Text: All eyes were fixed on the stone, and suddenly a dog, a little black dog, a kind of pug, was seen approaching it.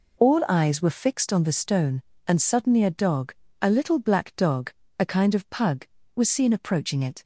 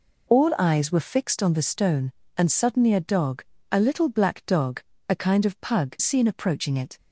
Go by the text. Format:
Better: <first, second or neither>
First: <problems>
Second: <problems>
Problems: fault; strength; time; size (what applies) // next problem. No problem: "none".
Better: first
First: none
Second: skips "was"; at 5.9 s